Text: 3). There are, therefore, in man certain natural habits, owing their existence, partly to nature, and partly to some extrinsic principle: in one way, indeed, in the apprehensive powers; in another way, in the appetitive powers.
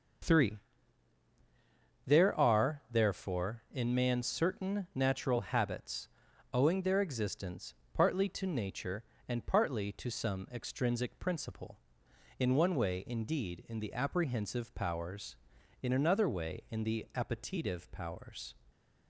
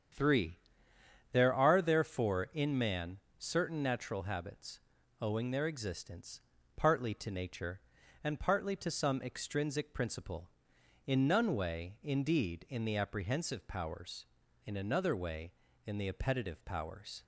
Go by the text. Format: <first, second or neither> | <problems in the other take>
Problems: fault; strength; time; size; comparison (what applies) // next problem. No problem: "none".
first | starts louder than the rest; strong; until 1.8 s; 8 dB; also in the first // pauses between "man" and "certain"; slight; at 3.1 s; 0.22 s long // says "none" for "one"; at 11.2 s